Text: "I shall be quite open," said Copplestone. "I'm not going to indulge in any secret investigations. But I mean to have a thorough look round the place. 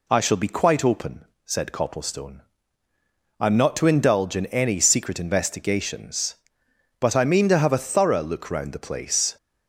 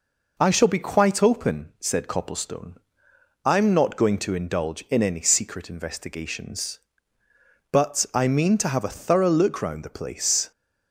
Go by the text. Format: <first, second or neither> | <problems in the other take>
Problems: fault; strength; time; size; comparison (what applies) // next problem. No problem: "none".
second | skips "going"; at 3.7 s